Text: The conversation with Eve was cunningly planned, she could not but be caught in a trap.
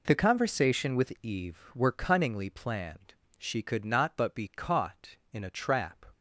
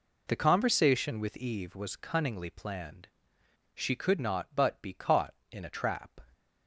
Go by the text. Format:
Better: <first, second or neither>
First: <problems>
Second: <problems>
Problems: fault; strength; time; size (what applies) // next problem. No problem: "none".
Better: second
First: says "were" for "was"; at 1.7 s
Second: none